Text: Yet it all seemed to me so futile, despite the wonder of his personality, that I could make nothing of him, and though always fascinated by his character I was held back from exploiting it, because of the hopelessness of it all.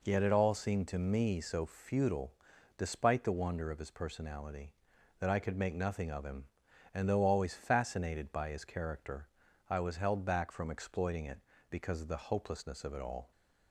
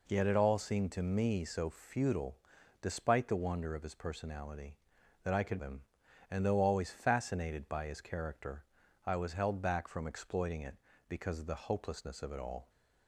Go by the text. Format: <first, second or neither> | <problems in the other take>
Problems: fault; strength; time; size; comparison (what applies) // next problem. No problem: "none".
first | skips "make nothing of"; at 5.6 s // pauses between "character" and "I"; at 8.6 s; 0.40 s long; also in the first